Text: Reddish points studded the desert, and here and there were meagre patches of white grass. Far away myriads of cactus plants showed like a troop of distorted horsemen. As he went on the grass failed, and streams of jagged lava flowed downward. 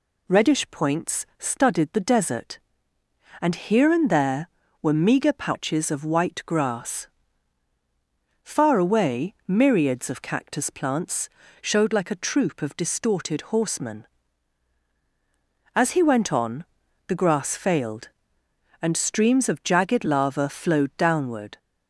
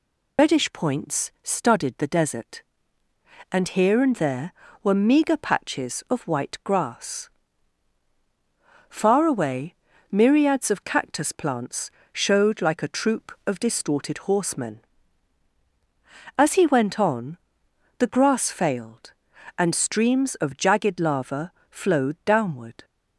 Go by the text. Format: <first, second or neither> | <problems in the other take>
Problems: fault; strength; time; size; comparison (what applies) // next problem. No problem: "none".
first | loses the start of "Reddish"; at 0.3 s; 85 ms // pauses between "away" and "myriads"; at 9.7 s; 0.38 s long // pauses between "plants" and "showed"; slight; at 11.9 s; 0.22 s long; slight in the first // pauses between "on" and "the"; noticeable; at 17.3 s; 0.58 s long; also in the first // pauses between "lava" and "flowed"; slight; at 21.5 s; 0.18 s long